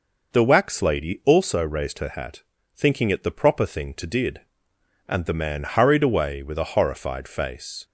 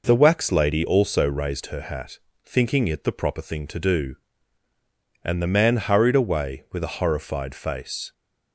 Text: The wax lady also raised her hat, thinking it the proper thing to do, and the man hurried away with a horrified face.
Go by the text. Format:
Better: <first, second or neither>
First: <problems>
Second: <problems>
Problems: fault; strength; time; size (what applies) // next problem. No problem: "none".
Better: second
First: says "did" for "do"; at 4.0 s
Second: none